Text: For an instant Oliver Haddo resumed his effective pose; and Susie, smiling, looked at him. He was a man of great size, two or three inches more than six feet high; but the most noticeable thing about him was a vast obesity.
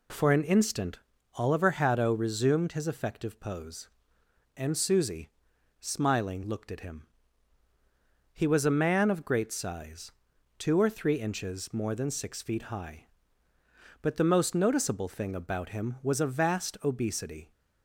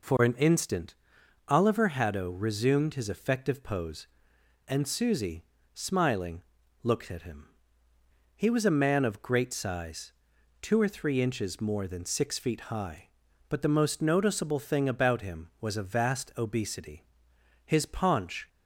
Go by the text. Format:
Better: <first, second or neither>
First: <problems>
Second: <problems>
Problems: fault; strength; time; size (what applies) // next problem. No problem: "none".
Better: first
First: pauses between "instant" and "Oliver"; slight; at 0.9 s; 0.36 s long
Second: pauses between "instant" and "Oliver"; noticeable; at 0.9 s; 0.54 s long // goes on to say "His paunch"; noticeable; from 17.6 s on; 0.82 s long